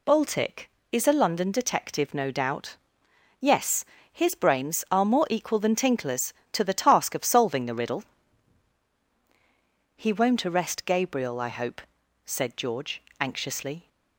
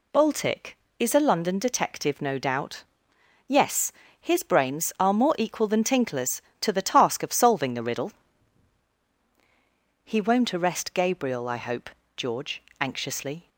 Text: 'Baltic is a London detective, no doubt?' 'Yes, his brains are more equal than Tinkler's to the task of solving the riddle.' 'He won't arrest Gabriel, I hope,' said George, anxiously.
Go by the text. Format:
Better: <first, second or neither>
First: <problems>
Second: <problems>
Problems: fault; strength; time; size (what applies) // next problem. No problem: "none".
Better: first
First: none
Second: skips "said"; at 12.0 s